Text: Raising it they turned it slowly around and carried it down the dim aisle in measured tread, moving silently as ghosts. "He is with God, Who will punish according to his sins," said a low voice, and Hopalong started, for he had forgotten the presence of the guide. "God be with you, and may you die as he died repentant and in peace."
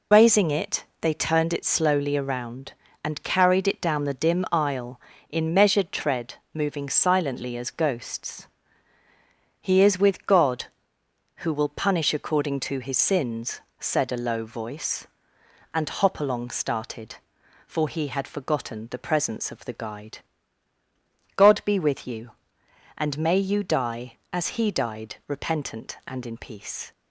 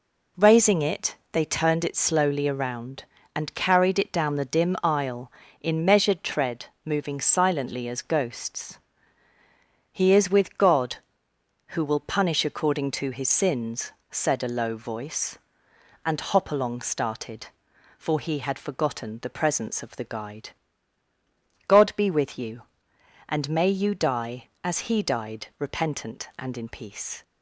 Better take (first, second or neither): second